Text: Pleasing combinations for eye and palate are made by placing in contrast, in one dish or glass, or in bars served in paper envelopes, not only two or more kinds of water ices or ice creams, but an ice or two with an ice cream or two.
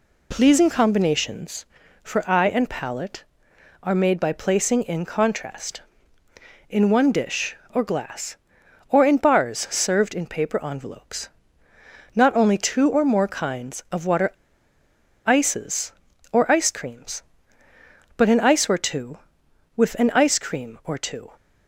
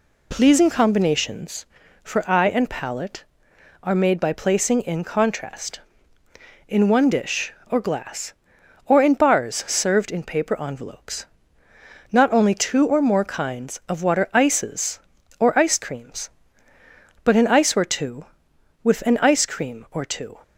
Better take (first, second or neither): second